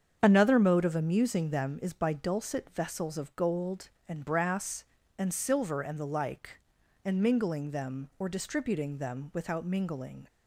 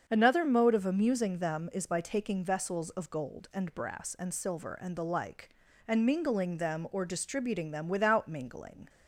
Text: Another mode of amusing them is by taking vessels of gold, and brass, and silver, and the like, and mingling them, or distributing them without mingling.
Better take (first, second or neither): second